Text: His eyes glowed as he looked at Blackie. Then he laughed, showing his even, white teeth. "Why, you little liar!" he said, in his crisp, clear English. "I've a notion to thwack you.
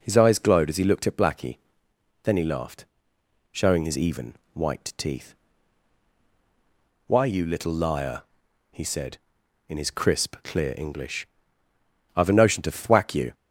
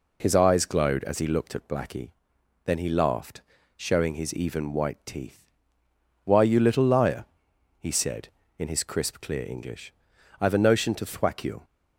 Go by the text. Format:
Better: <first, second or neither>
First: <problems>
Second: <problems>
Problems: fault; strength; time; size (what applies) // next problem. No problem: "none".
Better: neither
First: none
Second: none